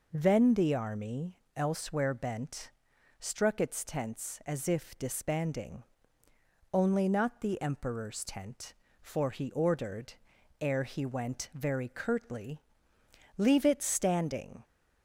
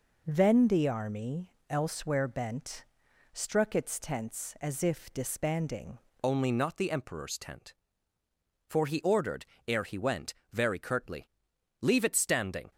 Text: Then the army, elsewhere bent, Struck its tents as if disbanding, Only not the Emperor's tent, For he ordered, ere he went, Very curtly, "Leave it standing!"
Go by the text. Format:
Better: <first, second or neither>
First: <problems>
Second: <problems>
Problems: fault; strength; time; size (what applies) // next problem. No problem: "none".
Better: first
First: none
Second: changes voice at "Only"; from 6.2 s on; 6.5 s long